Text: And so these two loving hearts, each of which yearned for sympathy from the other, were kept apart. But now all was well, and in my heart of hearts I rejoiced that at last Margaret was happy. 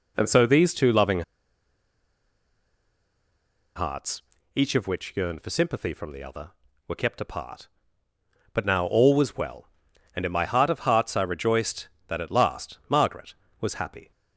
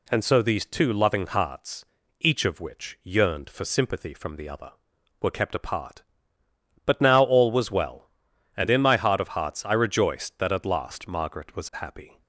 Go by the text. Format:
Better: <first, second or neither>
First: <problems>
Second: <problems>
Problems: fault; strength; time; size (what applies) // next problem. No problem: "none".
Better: second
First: pauses between "loving" and "hearts"; strong; at 1.2 s; 2.5 s long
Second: none